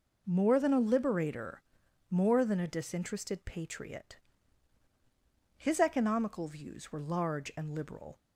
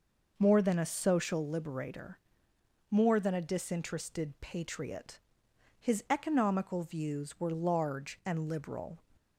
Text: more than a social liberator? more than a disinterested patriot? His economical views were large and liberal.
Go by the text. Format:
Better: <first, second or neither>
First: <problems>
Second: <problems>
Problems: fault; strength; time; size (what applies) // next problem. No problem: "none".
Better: second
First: skips "social"; at 0.8 s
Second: none